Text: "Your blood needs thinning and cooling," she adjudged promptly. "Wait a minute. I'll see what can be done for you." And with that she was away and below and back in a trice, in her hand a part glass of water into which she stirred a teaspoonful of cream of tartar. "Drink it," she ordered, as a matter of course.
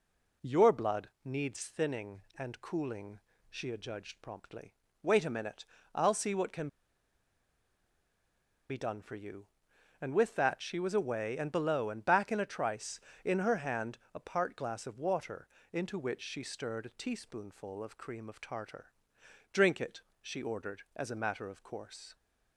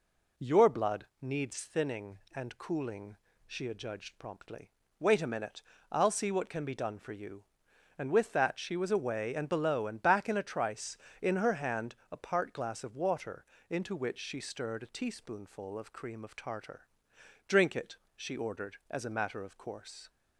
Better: second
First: pauses between "blood" and "needs"; slight; at 1.0 s; 0.16 s long // pauses between "can" and "be"; strong; at 6.6 s; 2.0 s long // pauses between "hand" and "a"; slight; at 13.9 s; 0.16 s long // pauses between "water" and "into"; slight; at 15.4 s; 0.24 s long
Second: pauses between "blood" and "needs"; slight; at 1.0 s; 0.16 s long // pauses between "hand" and "a"; slight; at 11.9 s; 0.16 s long // pauses between "water" and "into"; slight; at 13.4 s; 0.24 s long

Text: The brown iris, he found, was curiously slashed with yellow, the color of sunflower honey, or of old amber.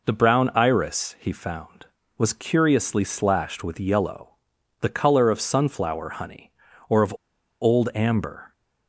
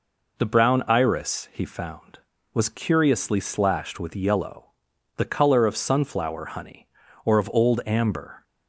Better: second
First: pauses between "of" and "old"; noticeable; at 7.1 s; 0.48 s long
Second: none

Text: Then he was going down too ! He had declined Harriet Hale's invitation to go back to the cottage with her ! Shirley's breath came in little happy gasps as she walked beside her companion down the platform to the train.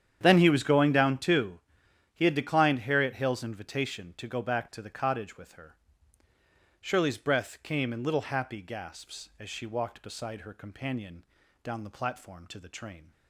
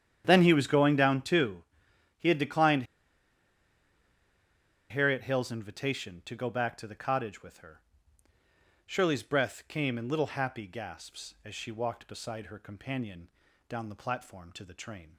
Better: first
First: starts louder than the rest; strong; until 1.2 s; 9 dB // pauses between "companion" and "down"; at 11.2 s; 0.40 s long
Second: starts louder than the rest; strong; until 1.2 s; 9 dB // pauses between "declined" and "Harriet"; strong; at 2.8 s; 2.0 s long // pauses between "companion" and "down"; at 13.2 s; 0.40 s long

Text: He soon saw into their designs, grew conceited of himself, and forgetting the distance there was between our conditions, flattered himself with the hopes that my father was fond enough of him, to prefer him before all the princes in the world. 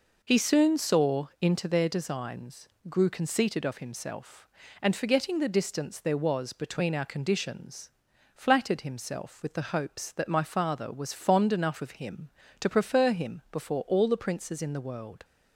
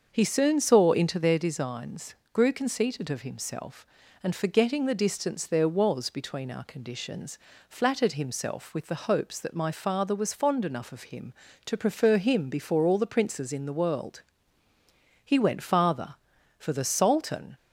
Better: first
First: none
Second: starts louder than the rest; until 1.1 s; 6.5 dB // goes on to say "He went farther for the sultan"; strong; from 15.2 s on; 2.3 s long

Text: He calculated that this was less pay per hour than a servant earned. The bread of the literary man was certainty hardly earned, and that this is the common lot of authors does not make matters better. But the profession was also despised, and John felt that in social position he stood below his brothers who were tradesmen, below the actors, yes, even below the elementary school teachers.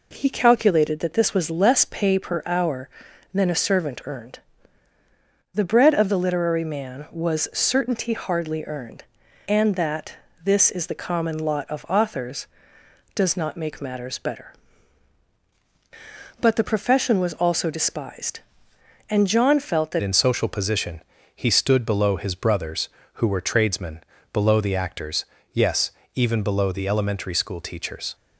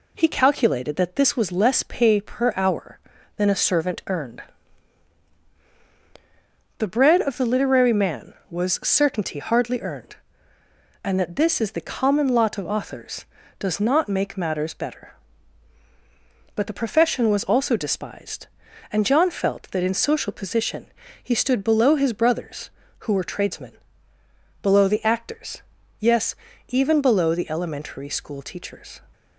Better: second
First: pauses between "that" and "this"; slight; at 10.1 s; 0.28 s long // changes voice at "in"; from 20.0 s on; 8.1 s long // pauses between "position" and "he"; slight; at 21.0 s; 0.34 s long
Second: pauses between "position" and "he"; slight; at 20.8 s; 0.36 s long

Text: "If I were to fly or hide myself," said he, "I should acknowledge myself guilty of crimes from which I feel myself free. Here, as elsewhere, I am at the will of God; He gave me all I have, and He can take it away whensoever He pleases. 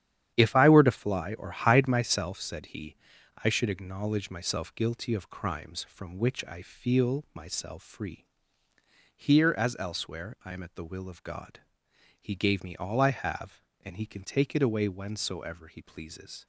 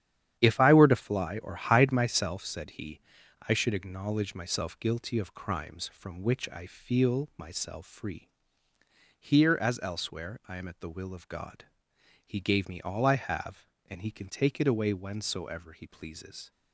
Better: neither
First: starts louder than the rest; strong; until 1.3 s; 10 dB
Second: starts louder than the rest; strong; until 1.4 s; 10 dB

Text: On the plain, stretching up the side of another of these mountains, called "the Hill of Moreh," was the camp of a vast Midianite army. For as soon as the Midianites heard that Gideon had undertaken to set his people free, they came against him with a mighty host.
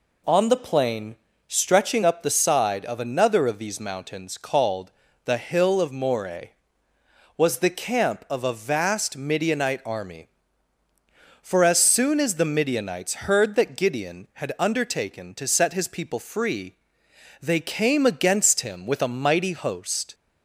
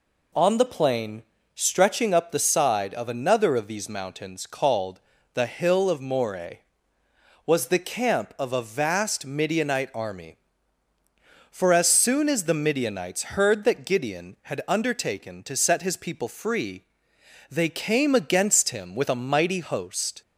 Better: neither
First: pauses between "called" and "the"; slight; at 4.9 s; 0.32 s long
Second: pauses between "called" and "the"; slight; at 5.0 s; 0.32 s long

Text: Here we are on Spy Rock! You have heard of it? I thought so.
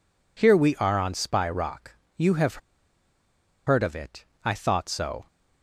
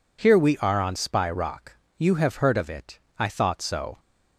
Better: second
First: pauses between "have" and "heard"; at 2.6 s; 1.0 s long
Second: none

